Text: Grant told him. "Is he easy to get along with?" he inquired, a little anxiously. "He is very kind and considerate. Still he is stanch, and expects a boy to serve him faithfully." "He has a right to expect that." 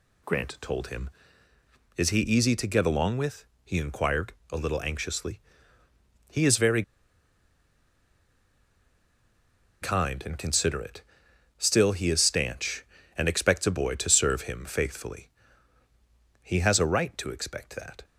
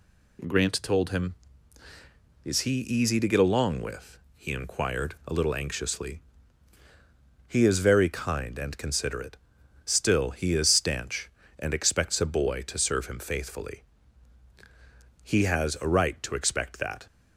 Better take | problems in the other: second | pauses between "very" and "kind"; strong; at 6.8 s; 3.0 s long

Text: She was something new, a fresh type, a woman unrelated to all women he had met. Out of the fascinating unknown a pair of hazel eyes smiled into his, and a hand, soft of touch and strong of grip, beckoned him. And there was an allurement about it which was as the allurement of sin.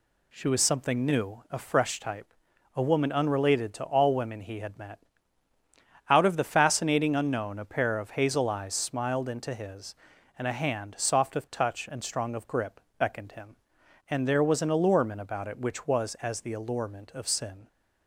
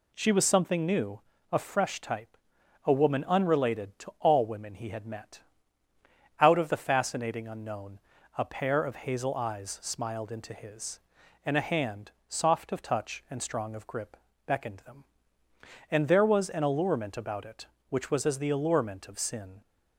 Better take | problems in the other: first | pauses between "unknown" and "a"; slight; at 7.9 s; 0.36 s long // says "them" for "him"; at 14.7 s

